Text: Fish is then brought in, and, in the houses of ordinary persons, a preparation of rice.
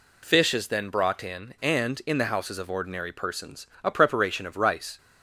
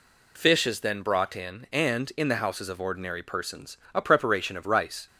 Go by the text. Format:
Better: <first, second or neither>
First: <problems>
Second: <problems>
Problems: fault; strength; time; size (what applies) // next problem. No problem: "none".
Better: neither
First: none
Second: none